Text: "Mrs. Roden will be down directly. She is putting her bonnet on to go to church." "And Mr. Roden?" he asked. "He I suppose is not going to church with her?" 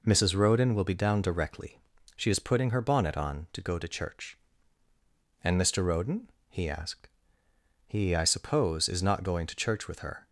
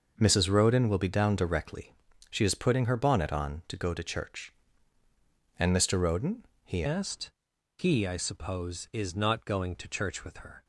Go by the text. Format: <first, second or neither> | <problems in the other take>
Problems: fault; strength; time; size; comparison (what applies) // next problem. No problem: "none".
first | changes voice at "asked"; from 6.8 s on; 3.8 s long